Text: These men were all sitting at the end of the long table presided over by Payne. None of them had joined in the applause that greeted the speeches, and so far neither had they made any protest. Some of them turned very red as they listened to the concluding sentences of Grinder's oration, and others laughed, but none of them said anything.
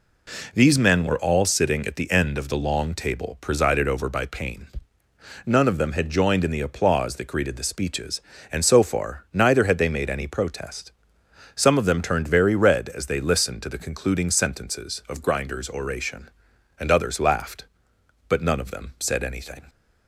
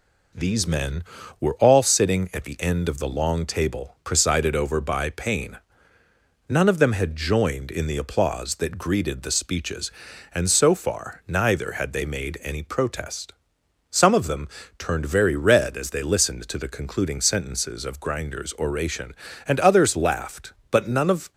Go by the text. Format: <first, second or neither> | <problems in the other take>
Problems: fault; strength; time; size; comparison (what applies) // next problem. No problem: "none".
first | pauses between "them" and "turned"; slight; at 14.4 s; 0.30 s long // stops before "them said anything"; at 21.3 s